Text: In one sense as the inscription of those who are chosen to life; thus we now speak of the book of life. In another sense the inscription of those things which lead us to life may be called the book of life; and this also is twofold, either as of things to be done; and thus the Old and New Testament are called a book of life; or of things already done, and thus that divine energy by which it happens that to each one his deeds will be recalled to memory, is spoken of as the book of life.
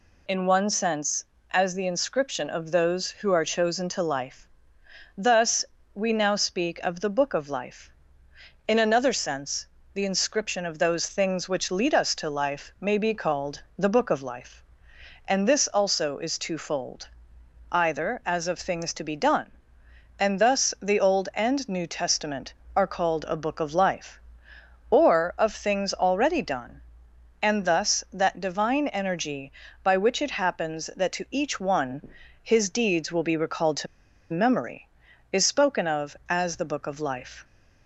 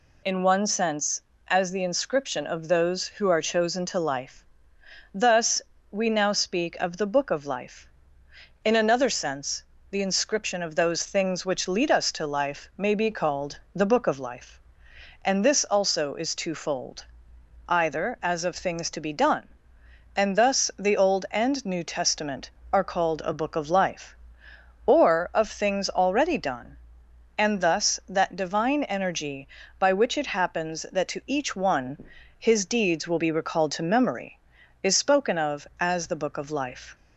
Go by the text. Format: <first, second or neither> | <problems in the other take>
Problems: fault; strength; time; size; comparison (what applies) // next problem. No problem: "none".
second | pauses between "thus" and "we"; slight; at 5.6 s; 0.30 s long; slight in the second // pauses between "sense" and "the"; slight; at 9.6 s; 0.26 s long; slight in the second // pauses between "one" and "his"; slight; at 32.0 s; 0.36 s long; slight in the second // pauses between "to" and "memory"; at 33.8 s; 0.45 s long